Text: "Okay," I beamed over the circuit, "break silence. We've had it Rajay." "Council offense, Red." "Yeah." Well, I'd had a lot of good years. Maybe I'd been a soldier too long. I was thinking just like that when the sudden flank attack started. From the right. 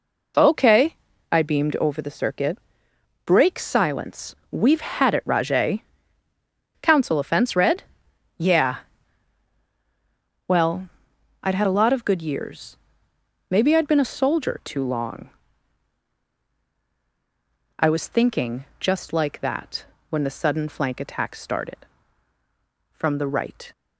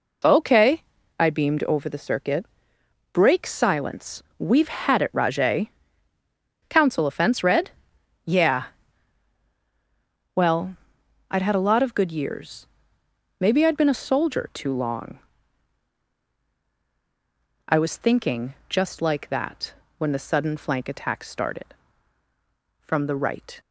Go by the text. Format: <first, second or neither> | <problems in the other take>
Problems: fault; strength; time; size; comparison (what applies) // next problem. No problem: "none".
neither | pauses between "that" and "when"; slight; the same in both